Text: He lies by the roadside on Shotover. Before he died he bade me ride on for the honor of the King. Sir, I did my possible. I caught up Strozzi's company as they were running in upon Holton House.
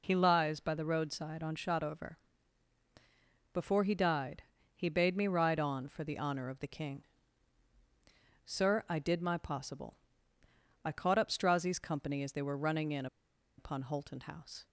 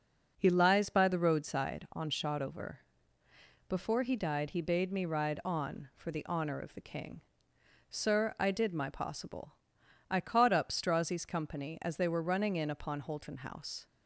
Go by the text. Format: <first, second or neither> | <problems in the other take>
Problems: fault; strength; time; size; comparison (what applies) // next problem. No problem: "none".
second | pauses between "died" and "he"; slight; at 4.4 s; 0.34 s long // pauses between "in" and "upon"; noticeable; at 13.0 s; 0.51 s long